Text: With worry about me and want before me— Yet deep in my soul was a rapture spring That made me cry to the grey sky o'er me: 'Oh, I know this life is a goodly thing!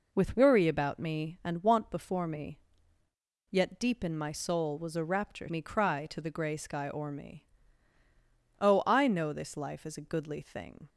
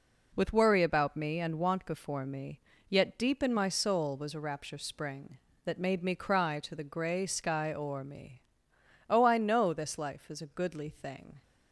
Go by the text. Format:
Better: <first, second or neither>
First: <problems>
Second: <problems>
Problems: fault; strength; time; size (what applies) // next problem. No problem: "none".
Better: second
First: skips "spring That made"; at 5.5 s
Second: none